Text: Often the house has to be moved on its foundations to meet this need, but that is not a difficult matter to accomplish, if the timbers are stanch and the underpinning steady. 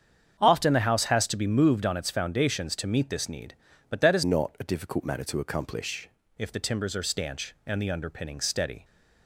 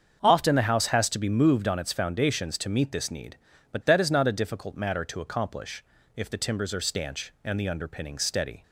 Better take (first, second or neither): second